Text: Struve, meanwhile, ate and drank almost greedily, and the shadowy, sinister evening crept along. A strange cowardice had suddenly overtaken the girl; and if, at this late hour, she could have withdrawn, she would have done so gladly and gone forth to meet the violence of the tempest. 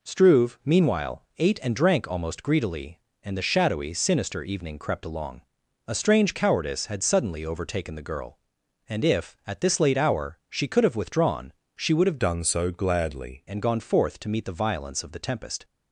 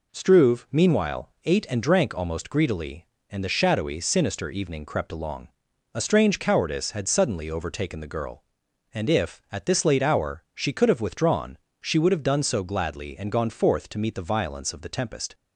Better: second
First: changes voice from "done" to "gladly"; from 12.1 to 13.4 s; 1.3 s long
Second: none

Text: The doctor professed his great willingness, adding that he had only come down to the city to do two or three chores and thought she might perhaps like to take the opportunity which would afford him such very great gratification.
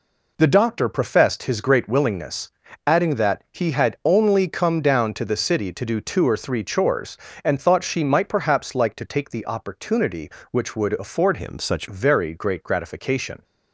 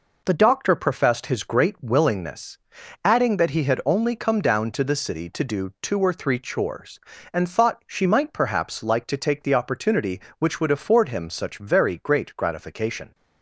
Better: second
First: changes voice from "him" to "such"; from 11.3 to 11.8 s; 0.5 s long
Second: none

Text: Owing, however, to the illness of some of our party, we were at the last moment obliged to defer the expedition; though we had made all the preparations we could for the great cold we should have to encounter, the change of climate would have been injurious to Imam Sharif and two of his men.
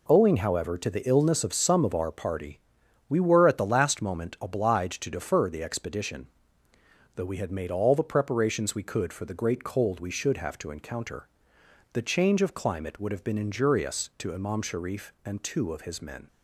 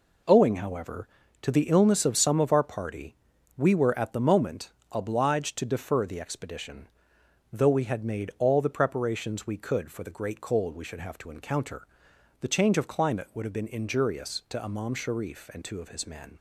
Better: first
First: none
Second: skips "last"; at 4.2 s // pauses between "moment" and "obliged"; slight; at 4.7 s; 0.22 s long

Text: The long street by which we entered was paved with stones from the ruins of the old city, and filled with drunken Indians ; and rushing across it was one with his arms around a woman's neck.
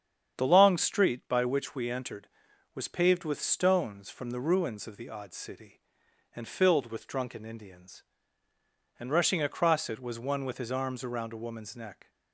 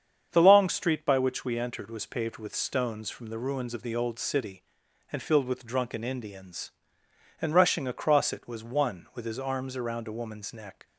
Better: second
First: starts louder than the rest; strong; until 1.4 s; 8 dB // says "odd" for "old"; at 5.0 s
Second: starts louder than the rest; strong; until 1.3 s; 7.5 dB

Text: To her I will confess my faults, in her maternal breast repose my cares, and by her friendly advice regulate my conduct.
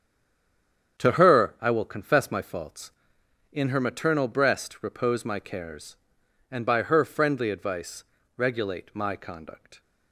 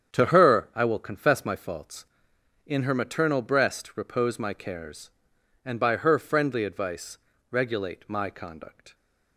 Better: second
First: stays silent before the first word; until 0.9 s; 0.9 s long // starts louder than the rest; strong; until 2.0 s; 8 dB // pauses between "advice" and "regulate"; slight; at 8.0 s; 0.32 s long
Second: starts louder than the rest; strong; until 1.1 s; 8 dB // pauses between "advice" and "regulate"; slight; at 7.1 s; 0.32 s long

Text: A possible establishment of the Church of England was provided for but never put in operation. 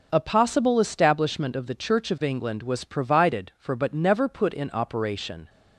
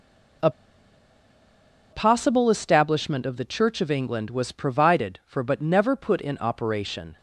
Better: first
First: none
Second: pauses between "A" and "possible"; strong; at 0.4 s; 1.4 s long

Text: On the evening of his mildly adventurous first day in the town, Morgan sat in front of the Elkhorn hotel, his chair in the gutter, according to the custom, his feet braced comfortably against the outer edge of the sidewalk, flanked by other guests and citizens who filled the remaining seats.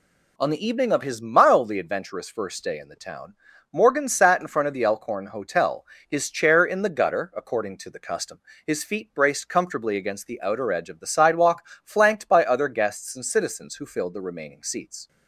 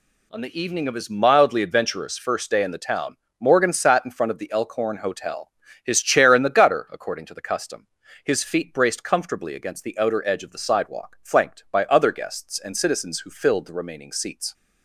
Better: neither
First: none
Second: none

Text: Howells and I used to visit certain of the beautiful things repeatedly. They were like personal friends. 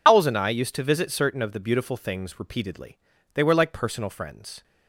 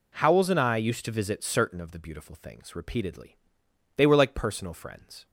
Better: second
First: loses the start of "Howells"; at 0.0 s; 110 ms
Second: none

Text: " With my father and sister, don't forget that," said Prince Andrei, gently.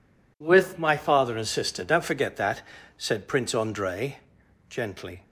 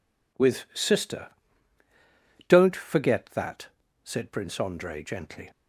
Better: first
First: none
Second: skips "my father and"; at 0.6 s

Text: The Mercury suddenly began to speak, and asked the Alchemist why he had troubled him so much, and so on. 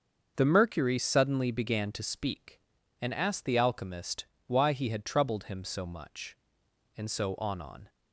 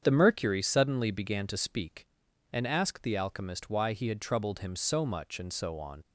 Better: second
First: starts louder than the rest; until 1.3 s; 6.5 dB // pauses between "Alchemist" and "why"; slight; at 4.2 s; 0.24 s long // says "on" twice; at 7.6 s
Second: starts louder than the rest; strong; until 1.0 s; 8 dB

